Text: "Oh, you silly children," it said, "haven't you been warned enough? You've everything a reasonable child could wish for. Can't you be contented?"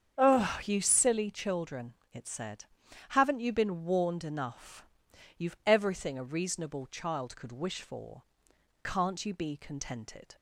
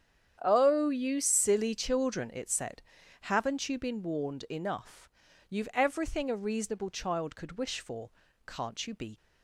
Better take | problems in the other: first | starts louder than the rest; strong; until 1.4 s; 8.5 dB; strong in the first // stops before "contented"; at 9.1 s

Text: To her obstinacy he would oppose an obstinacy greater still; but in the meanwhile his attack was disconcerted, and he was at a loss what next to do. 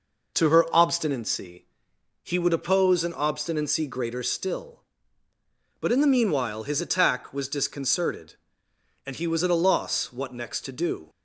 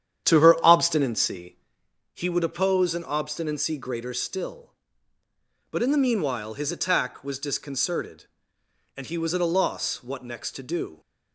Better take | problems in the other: first | starts louder than the rest; strong; until 1.7 s; 9.5 dB // pauses between "obstinacy" and "he"; noticeable; at 1.5 s; 0.58 s long; noticeable in the first

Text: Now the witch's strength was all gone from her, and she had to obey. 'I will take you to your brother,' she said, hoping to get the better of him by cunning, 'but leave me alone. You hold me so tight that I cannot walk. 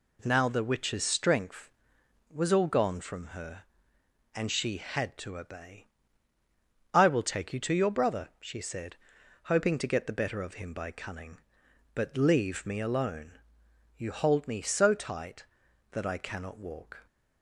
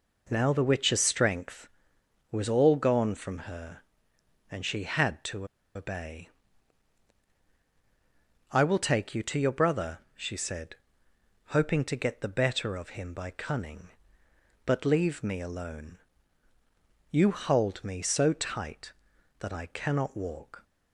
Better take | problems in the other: first | pauses between "to" and "obey"; slight; at 5.4 s; 0.28 s long

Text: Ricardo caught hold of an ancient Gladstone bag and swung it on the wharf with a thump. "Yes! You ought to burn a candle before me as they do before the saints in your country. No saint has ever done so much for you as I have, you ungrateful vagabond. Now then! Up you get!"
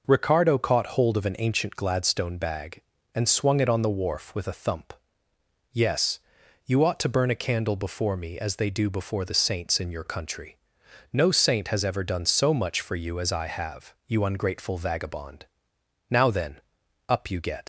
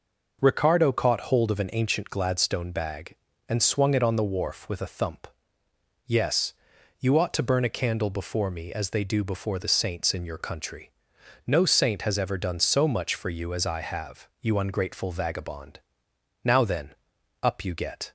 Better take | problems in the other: second | leaves "get" unfinished; at 17.6 s; 100 ms

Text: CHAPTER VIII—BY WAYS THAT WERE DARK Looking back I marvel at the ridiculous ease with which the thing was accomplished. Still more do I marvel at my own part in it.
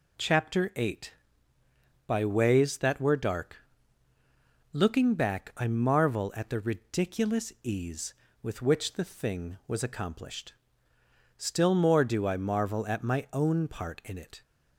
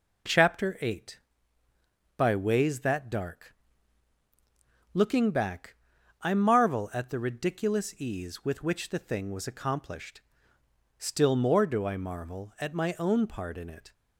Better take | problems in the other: first | skips "WERE"; at 3.0 s // pauses between "DARK" and "Looking"; strong; at 3.5 s; 1.3 s long; also in the first // pauses between "back" and "I"; at 5.7 s; 0.44 s long

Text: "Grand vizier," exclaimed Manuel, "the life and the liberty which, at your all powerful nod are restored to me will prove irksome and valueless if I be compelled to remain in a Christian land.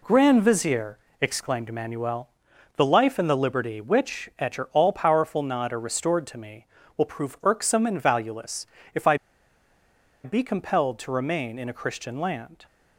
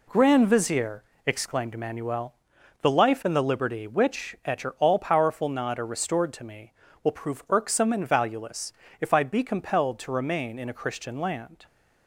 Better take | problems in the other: second | pauses between "valueless" and "if"; slight; at 8.6 s; 0.28 s long; slight in the second // pauses between "I" and "be"; at 9.1 s; 1.0 s long

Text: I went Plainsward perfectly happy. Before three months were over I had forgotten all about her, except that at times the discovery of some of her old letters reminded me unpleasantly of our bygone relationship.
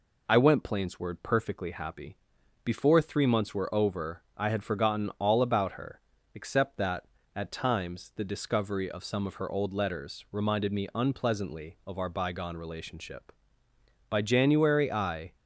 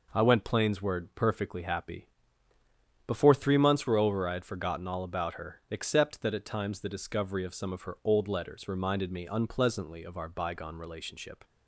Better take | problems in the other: second | goes on to say "By January I"; noticeable; from 14.0 s on; 1.2 s long

